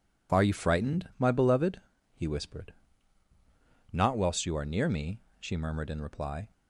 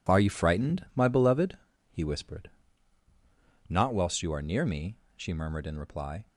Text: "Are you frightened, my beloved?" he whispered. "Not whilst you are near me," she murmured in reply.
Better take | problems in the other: first | gets quieter; strong; throughout; 9.5 dB

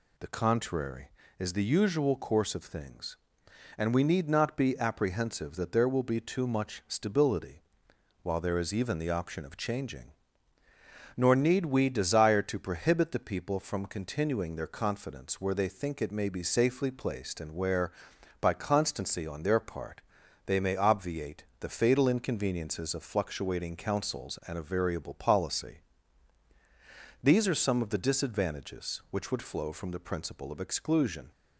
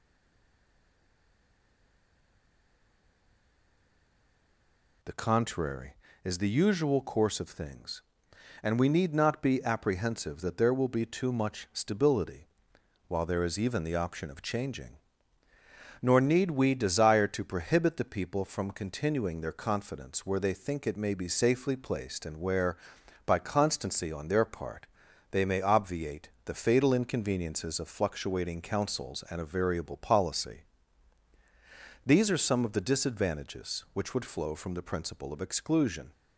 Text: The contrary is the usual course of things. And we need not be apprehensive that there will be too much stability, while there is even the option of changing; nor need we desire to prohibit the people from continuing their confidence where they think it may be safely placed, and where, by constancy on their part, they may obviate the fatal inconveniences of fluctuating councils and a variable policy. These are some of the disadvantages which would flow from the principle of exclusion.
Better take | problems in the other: first | stays silent before the first word; strong; until 5.0 s; 5.0 s long

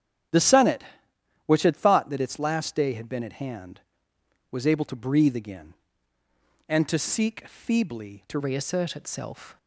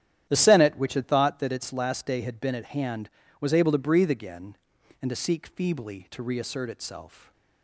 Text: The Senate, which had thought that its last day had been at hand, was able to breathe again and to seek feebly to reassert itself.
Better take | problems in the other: second | starts louder than the rest; strong; until 1.9 s; 10.5 dB; strong in the second // changes voice at "reassert"; from 8.3 s on; 1.2 s long

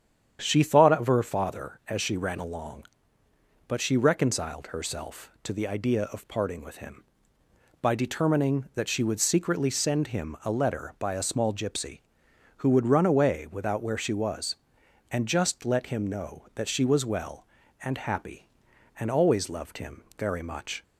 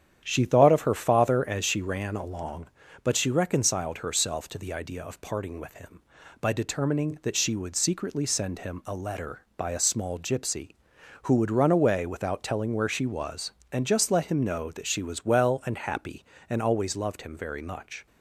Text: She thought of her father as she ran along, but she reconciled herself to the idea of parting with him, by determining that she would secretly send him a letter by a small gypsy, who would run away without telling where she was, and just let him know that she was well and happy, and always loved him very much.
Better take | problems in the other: second | starts louder than the rest; strong; until 1.4 s; 8.5 dB; strong in the second // skips "telling"; at 13.8 s

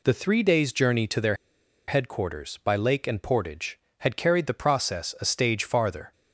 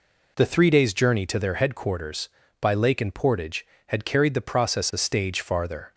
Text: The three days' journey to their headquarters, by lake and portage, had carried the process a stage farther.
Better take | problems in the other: second | pauses between "their" and "headquarters"; noticeable; at 1.3 s; 0.53 s long

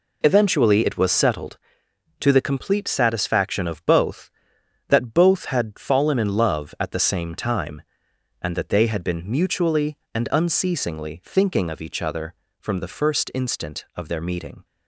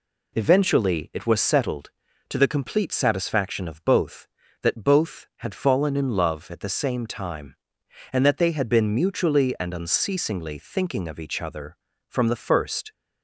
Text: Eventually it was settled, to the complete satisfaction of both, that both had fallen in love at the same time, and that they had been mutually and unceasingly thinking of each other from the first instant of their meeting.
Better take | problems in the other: first | stops before "instant of their meeting"; at 12.9 s

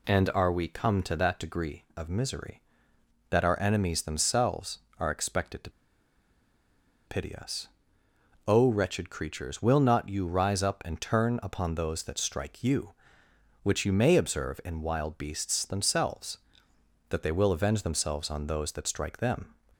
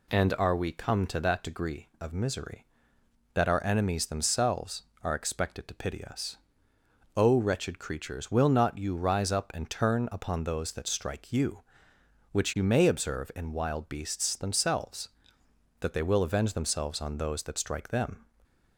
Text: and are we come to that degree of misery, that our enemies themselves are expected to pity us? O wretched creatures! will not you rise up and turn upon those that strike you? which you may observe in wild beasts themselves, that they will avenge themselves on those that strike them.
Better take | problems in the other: second | pauses between "to" and "pity"; strong; at 5.6 s; 1.3 s long

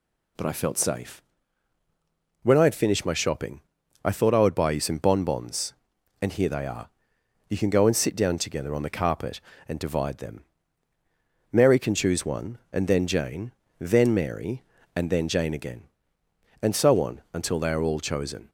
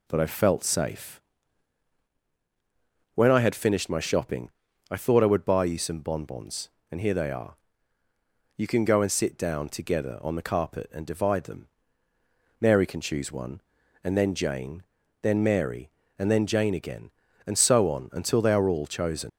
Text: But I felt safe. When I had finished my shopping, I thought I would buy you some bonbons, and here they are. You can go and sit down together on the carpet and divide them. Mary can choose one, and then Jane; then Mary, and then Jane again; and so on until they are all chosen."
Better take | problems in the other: first | leaves "chosen" unfinished; at 19.2 s; 120 ms

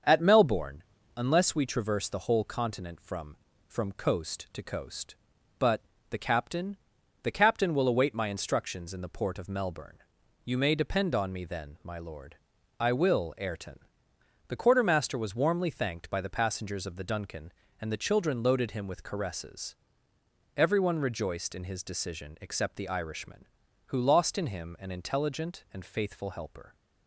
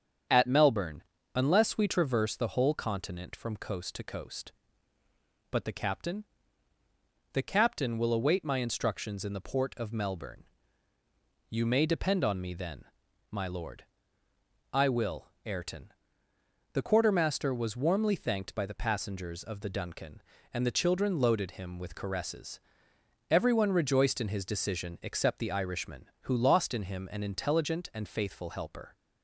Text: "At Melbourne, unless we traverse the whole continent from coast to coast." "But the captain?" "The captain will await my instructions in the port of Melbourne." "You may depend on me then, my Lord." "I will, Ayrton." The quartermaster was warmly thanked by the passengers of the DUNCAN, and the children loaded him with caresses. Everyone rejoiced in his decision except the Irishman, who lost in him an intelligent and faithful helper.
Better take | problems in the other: second | starts louder than the rest; until 1.4 s; 7 dB; strong in the second // says "from" twice; at 3.6 s // pauses between "But" and "the"; slight; at 5.8 s; 0.30 s long

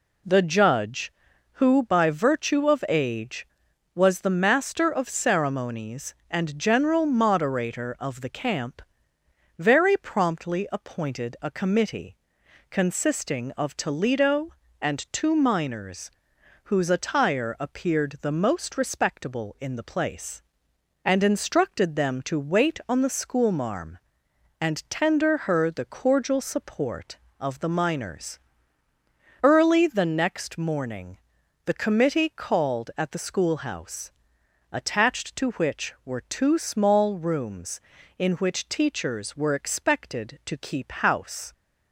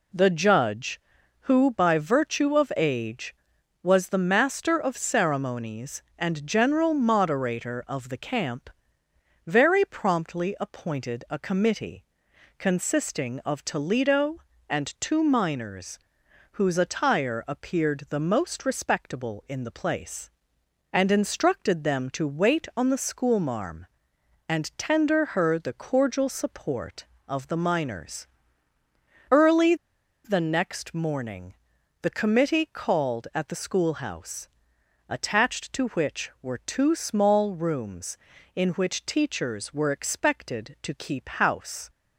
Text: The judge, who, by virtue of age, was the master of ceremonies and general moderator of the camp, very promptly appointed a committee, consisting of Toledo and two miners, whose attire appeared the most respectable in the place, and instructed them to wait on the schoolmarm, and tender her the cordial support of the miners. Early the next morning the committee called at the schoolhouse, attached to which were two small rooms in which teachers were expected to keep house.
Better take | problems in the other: first | pauses between "Early" and "the"; noticeable; at 29.7 s; 0.50 s long // pauses between "morning" and "the"; noticeable; at 31.5 s; 0.48 s long; noticeable in the first

